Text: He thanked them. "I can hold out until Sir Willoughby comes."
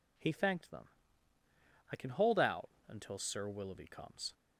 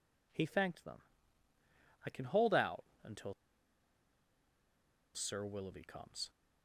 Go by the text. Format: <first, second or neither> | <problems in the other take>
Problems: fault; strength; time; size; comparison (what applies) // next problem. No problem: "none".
first | pauses between "out" and "until"; slight; at 2.8 s; 0.18 s long; slight in the first // pauses between "until" and "Sir"; strong; at 3.3 s; 1.8 s long